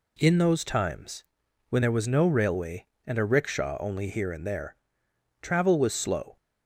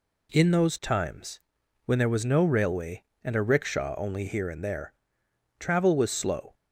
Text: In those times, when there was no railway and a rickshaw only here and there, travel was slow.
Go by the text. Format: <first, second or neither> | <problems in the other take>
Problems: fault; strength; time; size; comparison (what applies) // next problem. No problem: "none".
neither | none